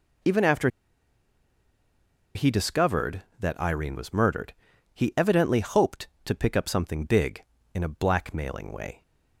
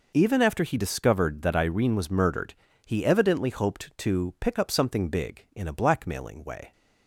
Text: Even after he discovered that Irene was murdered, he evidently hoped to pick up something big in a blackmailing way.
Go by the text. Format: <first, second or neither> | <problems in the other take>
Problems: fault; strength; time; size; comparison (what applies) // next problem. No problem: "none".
second | pauses between "after" and "he"; strong; at 0.6 s; 1.6 s long